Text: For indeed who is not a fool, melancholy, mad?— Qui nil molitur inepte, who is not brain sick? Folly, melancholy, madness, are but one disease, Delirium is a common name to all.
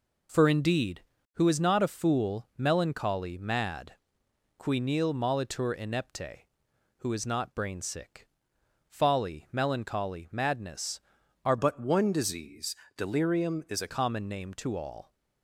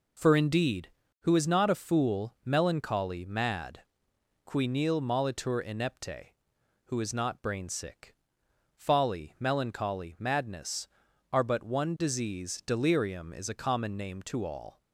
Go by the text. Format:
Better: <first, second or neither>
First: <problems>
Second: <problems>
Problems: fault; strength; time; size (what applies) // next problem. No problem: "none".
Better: second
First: changes voice from "but" to "a"; from 11.5 to 13.8 s; 2.3 s long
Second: none